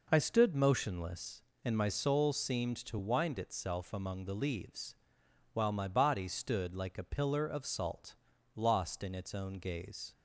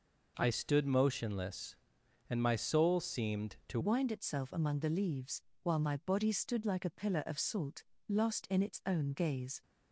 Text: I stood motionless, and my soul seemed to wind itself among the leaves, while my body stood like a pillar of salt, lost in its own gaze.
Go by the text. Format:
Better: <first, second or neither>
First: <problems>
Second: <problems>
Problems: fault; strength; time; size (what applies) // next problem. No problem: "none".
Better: first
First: none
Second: changes voice at "wind"; from 3.8 s on; 5.8 s long